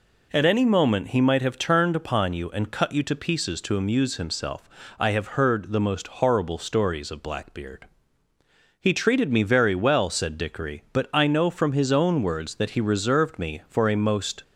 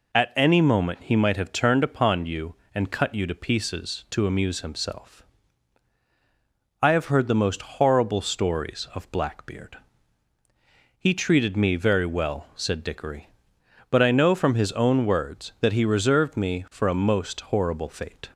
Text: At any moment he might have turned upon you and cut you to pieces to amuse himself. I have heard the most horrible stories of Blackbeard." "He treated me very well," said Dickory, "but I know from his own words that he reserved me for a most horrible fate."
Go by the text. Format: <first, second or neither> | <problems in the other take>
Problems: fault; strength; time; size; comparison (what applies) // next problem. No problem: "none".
second | stops before "horrible fate"; at 14.4 s